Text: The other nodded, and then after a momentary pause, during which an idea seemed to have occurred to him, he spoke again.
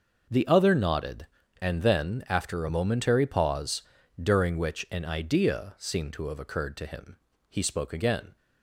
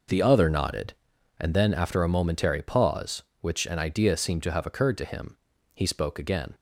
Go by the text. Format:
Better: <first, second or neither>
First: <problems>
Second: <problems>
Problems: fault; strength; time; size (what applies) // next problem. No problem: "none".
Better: first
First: none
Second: skips "during"; at 3.3 s